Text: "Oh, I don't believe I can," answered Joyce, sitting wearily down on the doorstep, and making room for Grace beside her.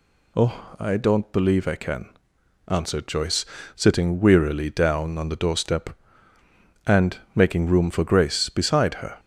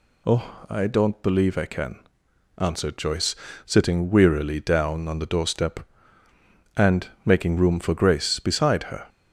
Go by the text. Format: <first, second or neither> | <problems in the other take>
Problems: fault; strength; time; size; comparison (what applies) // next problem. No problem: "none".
neither | pauses between "and" and "making"; slight; the same in both